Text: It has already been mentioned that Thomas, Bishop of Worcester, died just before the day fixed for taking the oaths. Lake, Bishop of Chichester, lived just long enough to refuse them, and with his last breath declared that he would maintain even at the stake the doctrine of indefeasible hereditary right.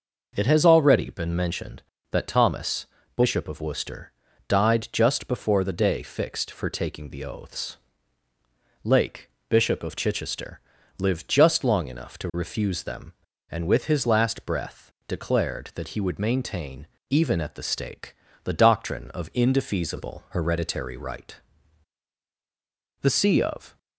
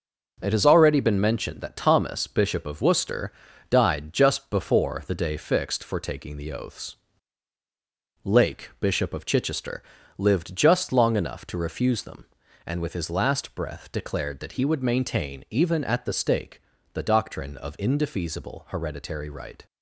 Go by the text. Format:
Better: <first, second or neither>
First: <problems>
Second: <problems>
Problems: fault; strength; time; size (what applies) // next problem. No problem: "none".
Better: second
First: pauses between "breath" and "declared"; slight; at 14.9 s; 0.16 s long // pauses between "maintain" and "even"; slight; at 16.8 s; 0.24 s long // pauses between "stake" and "the"; slight; at 18.1 s; 0.30 s long // goes on to say "The see of"; noticeable; from 23.0 s on; 0.76 s long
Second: pauses between "stake" and "the"; slight; at 16.6 s; 0.32 s long